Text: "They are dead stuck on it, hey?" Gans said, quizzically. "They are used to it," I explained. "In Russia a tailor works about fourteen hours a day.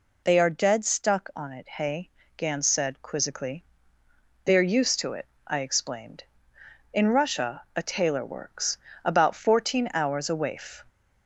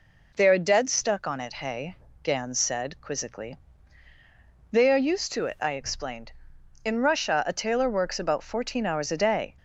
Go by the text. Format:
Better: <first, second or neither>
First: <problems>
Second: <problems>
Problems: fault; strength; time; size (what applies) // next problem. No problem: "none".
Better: second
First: pauses between "works" and "about"; slight; at 8.7 s; 0.26 s long // says "waif" for "day"; at 10.3 s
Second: none